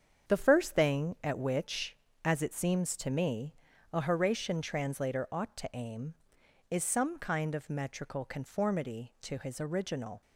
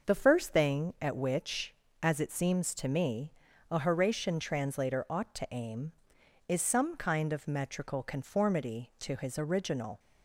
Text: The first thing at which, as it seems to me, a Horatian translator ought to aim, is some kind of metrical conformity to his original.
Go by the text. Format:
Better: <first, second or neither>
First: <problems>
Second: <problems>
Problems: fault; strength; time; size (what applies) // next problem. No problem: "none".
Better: second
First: gets quieter; strong; throughout; 8.5 dB // starts louder than the rest; strong; until 1.3 s; 7.5 dB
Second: starts louder than the rest; noticeable; until 1.1 s; 6 dB